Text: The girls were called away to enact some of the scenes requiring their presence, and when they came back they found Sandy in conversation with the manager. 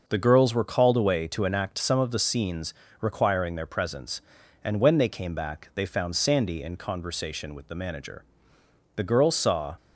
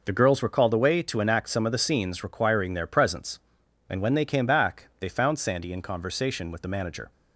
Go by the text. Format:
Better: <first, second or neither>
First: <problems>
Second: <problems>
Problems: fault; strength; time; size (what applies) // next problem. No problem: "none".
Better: second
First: pauses between "scenes" and "requiring"; slight; at 2.7 s; 0.28 s long // goes on to say "The girls saw"; noticeable; from 8.9 s on; 0.82 s long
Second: none